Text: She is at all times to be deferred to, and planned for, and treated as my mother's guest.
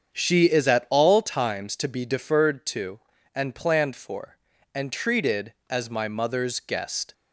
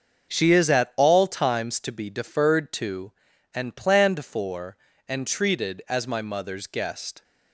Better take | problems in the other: neither | starts louder than the rest; the same in both

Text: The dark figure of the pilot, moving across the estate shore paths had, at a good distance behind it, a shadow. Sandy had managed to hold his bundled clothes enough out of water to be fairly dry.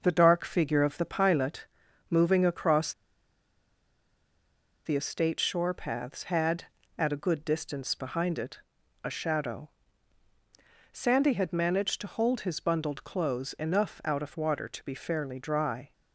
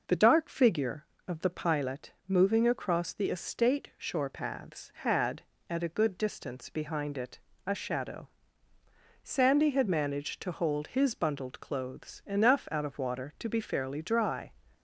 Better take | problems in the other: second | pauses between "across" and "the"; strong; at 2.9 s; 1.9 s long

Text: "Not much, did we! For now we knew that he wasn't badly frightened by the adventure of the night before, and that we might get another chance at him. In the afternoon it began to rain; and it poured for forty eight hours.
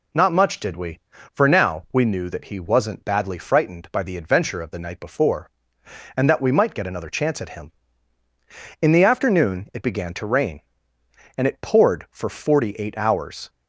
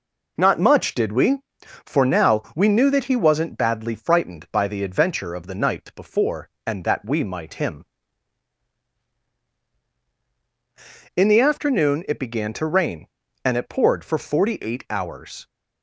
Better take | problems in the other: first | skips "get another chance at"; at 7.5 s

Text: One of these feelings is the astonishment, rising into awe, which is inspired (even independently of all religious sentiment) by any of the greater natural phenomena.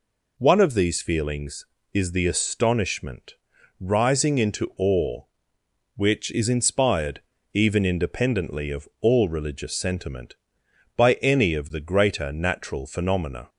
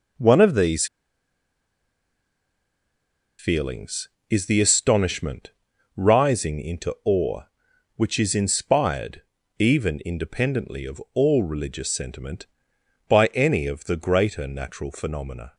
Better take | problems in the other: first | pauses between "these" and "feelings"; strong; at 0.8 s; 2.5 s long

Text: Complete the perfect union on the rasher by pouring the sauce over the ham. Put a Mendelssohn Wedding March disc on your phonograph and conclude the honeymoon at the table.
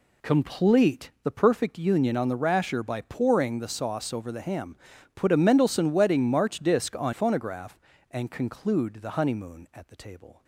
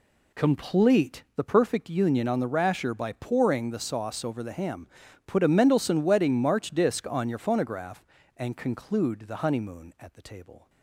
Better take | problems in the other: second | skips "your"; at 7.1 s

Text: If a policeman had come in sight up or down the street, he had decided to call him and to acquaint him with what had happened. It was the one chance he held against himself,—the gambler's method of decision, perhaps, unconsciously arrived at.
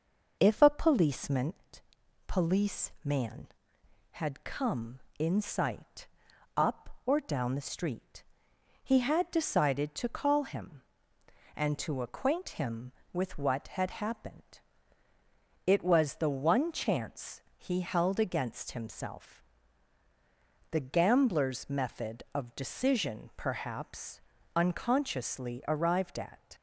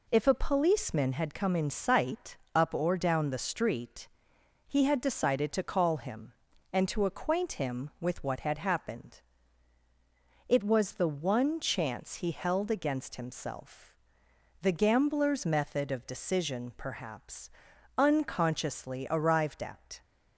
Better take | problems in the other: second | says "policeman" twice; at 2.2 s // pauses between "sight" and "up"; noticeable; at 6.0 s; 0.50 s long; slight in the second // pauses between "chance" and "he"; slight; at 17.3 s; 0.18 s long

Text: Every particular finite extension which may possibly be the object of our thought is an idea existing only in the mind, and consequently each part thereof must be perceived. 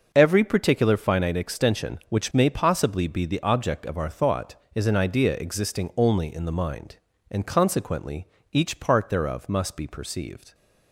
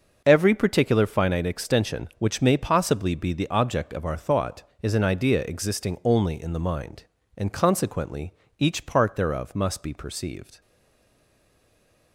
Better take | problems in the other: first | starts louder than the rest; noticeable; until 1.2 s; 6 dB // pauses between "consequently" and "each"; slight; at 8.3 s; 0.24 s long; slight in the first // stays silent after the last word; noticeable; from 10.6 s on; 1.5 s long

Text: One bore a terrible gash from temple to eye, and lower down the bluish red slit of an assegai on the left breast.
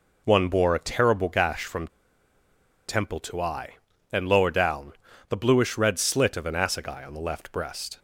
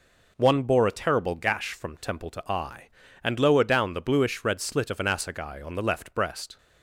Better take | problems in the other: second | pauses between "from" and "temple"; at 1.8 s; 0.99 s long // pauses between "down" and "the"; at 4.9 s; 0.38 s long

